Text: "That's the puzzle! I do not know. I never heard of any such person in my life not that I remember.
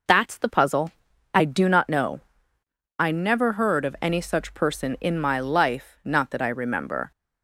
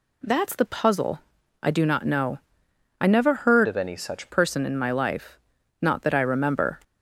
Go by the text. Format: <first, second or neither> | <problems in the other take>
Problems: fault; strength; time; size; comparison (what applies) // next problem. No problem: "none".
first | changes voice from "of" to "such"; from 3.6 to 4.2 s; 0.6 s long // pauses between "life" and "not"; noticeable; at 5.3 s; 0.46 s long